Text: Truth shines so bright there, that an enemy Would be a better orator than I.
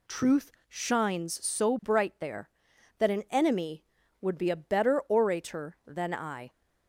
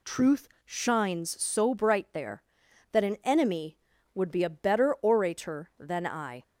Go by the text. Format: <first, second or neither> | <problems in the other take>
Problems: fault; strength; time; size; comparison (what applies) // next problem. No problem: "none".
neither | pauses between "Truth" and "shines"; slight; the same in both